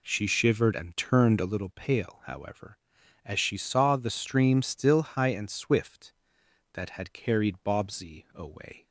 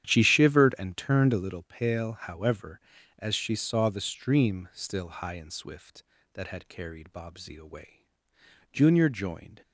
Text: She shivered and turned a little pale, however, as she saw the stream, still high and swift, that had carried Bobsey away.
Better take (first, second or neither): first